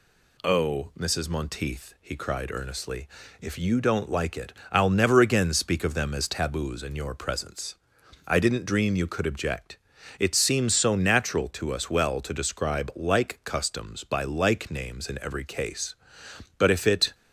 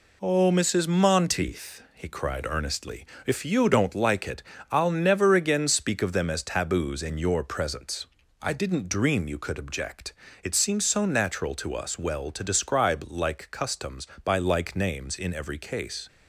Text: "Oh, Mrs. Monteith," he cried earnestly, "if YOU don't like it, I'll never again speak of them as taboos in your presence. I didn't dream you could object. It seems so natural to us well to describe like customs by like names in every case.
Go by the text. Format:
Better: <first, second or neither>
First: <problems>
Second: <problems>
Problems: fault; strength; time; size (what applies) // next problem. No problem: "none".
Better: second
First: goes on to say "But if it"; from 16.5 s on; 0.58 s long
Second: none